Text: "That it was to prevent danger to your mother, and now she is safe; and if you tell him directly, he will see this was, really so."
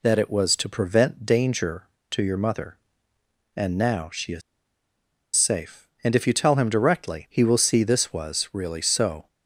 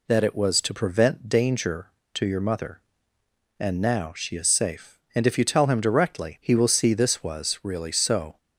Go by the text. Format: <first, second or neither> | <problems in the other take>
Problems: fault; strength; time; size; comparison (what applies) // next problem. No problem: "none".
second | pauses between "is" and "safe"; noticeable; at 4.4 s; 0.95 s long